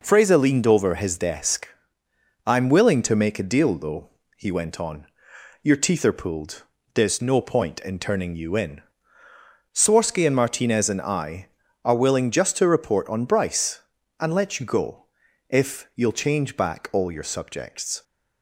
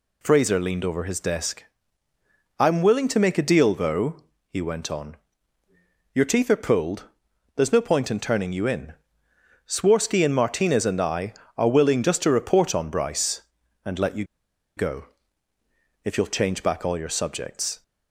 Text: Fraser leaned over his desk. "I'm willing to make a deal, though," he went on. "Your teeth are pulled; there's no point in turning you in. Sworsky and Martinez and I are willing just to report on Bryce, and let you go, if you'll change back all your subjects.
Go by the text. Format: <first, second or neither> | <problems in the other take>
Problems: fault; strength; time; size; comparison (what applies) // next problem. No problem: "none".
first | pauses between "you" and "go"; noticeable; at 14.2 s; 0.52 s long